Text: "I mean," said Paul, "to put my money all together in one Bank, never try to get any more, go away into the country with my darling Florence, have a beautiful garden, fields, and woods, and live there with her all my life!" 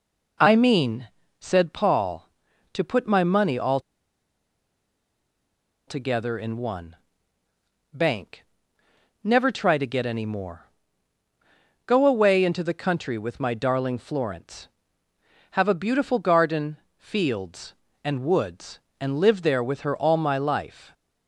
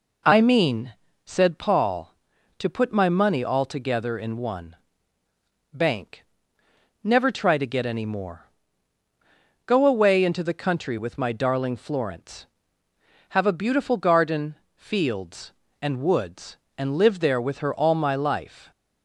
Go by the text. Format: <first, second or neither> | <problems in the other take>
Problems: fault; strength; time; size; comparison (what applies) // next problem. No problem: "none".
second | pauses between "all" and "together"; strong; at 3.7 s; 2.0 s long // pauses between "one" and "Bank"; noticeable; at 6.9 s; 0.96 s long; noticeable in the second